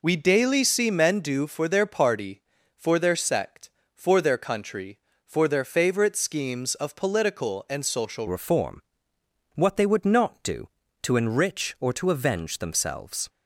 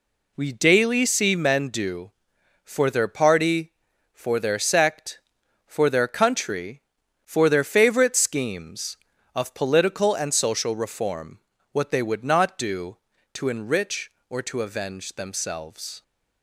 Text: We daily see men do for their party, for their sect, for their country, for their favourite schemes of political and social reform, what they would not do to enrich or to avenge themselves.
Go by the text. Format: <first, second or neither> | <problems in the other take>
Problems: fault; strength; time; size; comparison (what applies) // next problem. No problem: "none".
second | changes voice at "reform"; from 8.2 s on; 5.0 s long